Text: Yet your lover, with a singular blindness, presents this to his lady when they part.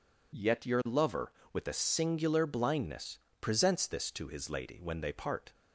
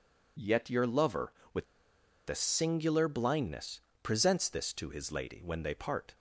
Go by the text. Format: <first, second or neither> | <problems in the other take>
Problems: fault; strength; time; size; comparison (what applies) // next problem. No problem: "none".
first | pauses between "with" and "a"; noticeable; at 1.6 s; 0.63 s long